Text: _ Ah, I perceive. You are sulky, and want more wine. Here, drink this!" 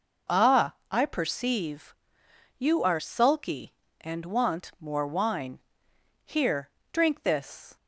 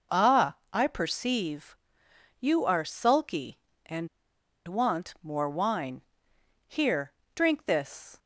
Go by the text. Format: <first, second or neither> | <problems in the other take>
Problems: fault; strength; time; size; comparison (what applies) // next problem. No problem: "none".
first | pauses between "and" and "want"; noticeable; at 4.0 s; 0.60 s long